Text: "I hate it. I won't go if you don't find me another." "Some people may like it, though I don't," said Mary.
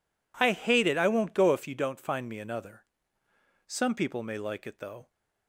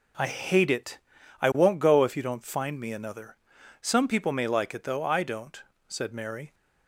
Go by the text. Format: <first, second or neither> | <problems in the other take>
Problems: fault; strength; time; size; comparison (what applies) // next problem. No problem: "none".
second | stops before "I don't said Mary"; at 5.1 s